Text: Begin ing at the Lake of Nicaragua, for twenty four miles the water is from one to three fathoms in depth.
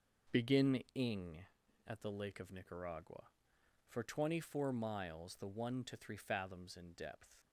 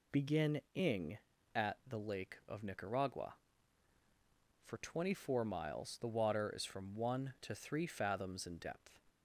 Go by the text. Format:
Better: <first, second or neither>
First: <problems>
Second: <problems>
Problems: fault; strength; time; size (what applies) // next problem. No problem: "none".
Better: second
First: starts louder than the rest; noticeable; until 1.4 s; 6 dB // skips "water is from"; at 5.4 s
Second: none